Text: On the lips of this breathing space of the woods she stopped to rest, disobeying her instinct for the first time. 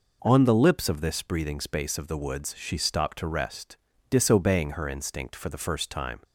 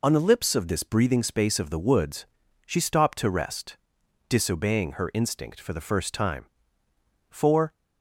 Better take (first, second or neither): first